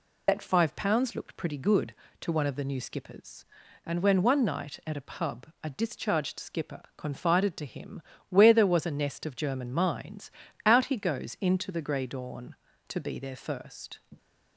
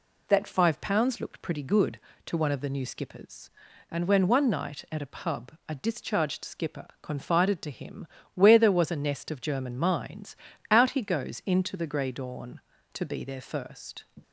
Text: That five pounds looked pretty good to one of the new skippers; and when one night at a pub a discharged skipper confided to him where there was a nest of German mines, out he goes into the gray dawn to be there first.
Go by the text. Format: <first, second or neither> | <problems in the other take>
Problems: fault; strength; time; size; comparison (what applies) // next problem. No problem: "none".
second | loses the start of "That"; at 0.2 s; 45 ms // pauses between "him" and "where"; slight; at 8.0 s; 0.26 s long; slight in the second